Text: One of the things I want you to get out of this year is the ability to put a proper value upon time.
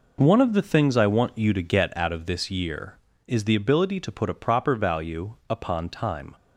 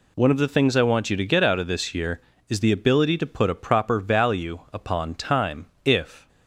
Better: first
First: none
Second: goes on to say "If"; slight; from 5.8 s on; 0.44 s long

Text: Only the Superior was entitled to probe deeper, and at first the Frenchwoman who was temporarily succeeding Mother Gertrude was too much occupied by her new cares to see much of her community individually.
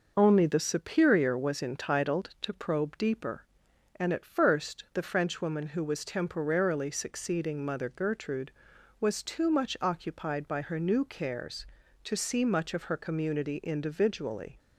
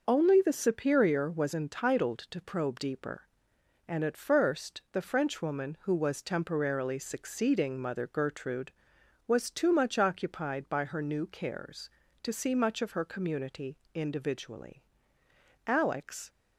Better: first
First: none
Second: pauses between "community" and "individually"; slight; at 13.7 s; 0.16 s long // goes on to say "Alex"; noticeable; from 15.6 s on; 0.66 s long

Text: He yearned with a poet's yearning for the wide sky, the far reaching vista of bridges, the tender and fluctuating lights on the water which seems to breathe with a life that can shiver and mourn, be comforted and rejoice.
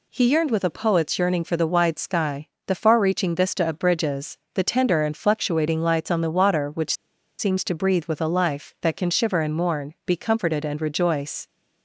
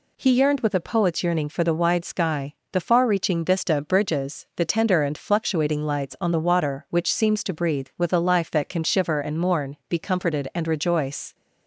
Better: second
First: pauses between "which" and "seems"; at 6.9 s; 0.44 s long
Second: none

